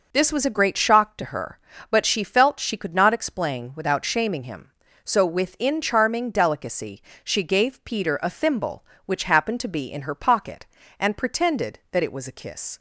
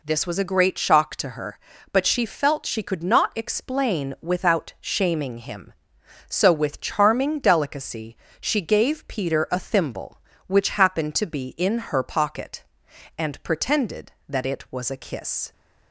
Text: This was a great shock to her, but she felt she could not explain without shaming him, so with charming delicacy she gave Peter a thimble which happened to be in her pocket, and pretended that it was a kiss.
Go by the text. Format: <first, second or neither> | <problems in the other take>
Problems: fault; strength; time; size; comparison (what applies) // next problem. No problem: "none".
second | says "within" for "with"; at 5.2 s // pauses between "delicacy" and "she"; slight; at 7.0 s; 0.22 s long; slight in the second